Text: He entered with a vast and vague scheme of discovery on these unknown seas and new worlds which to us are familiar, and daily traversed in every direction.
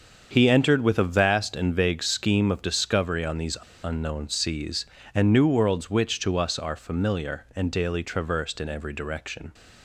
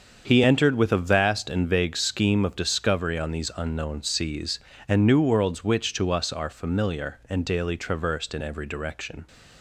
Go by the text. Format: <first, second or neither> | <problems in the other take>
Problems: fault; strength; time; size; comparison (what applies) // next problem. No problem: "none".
second | starts louder than the rest; until 1.3 s; 7 dB; also in the second // pauses between "these" and "unknown"; slight; at 3.5 s; 0.25 s long